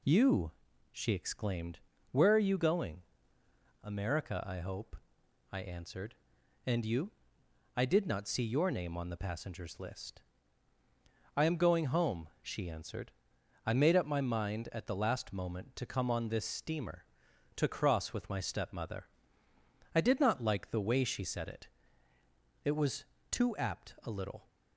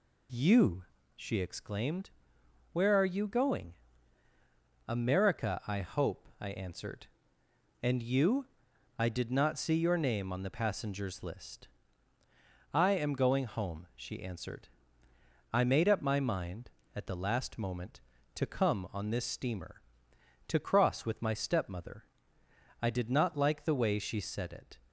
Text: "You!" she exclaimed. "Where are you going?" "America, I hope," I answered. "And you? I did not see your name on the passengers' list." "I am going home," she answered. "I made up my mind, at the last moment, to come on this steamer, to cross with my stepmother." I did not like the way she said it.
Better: second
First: goes on to say "It was too apt a little"; strong; from 22.6 s on; 1.8 s long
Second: none

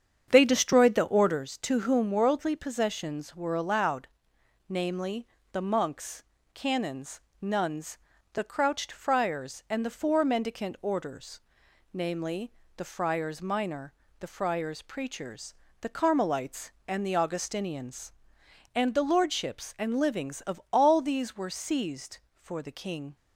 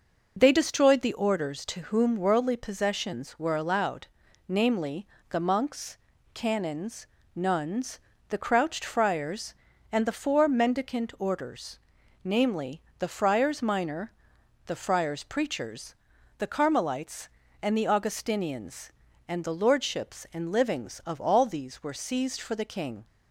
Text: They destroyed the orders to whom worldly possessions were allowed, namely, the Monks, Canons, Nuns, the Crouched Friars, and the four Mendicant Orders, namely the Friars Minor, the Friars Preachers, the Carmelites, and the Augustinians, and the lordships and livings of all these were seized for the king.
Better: second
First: starts louder than the rest; strong; until 1.5 s; 8 dB // pauses between "namely" and "the"; slight; at 12.5 s; 0.26 s long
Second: pauses between "namely" and "the"; slight; at 12.8 s; 0.18 s long

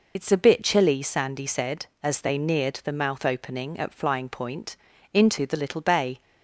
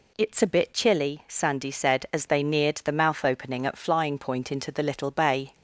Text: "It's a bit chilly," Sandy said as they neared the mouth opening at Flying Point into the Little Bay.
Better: second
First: loses the start of "It's"; at 0.1 s; 55 ms // pauses between "Point" and "into"; slight; at 4.7 s; 0.36 s long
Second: none

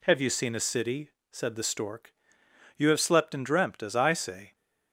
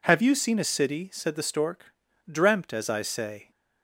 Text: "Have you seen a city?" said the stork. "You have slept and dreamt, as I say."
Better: first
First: none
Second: skips "You have slept and"; at 2.1 s

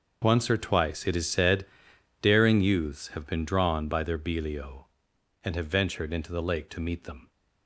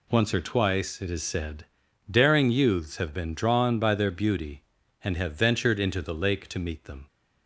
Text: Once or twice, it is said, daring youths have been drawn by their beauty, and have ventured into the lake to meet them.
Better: second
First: starts louder than the rest; noticeable; until 1.2 s; 6 dB // says "belio" for "beauty"; at 4.1 s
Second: none

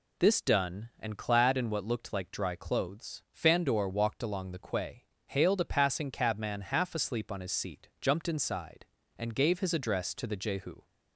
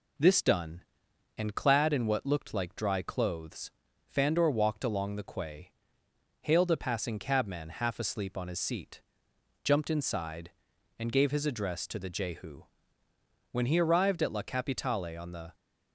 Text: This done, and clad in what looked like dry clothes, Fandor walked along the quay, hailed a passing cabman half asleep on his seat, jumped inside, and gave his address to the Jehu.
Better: first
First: none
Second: goes on to say "When he arrived at La Capitale on the"; strong; from 13.5 s on; 2.0 s long

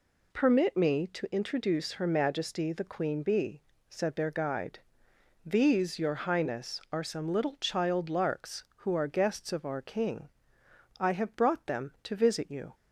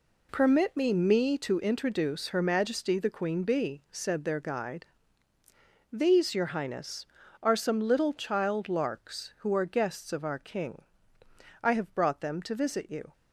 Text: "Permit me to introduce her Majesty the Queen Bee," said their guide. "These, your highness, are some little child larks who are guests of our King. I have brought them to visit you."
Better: first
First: none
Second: says "me" twice; at 0.9 s

